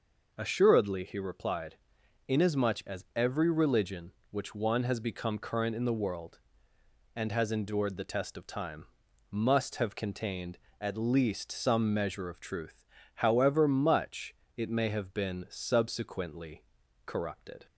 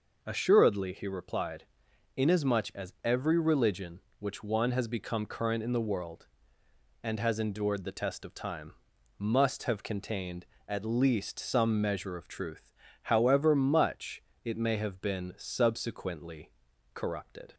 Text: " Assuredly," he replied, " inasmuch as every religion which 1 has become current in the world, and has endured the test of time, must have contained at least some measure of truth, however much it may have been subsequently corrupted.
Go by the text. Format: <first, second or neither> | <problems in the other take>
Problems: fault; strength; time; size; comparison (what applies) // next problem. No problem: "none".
neither | pauses between "much" and "it"; slight; the same in both // pauses between "subsequently" and "corrupted"; the same in both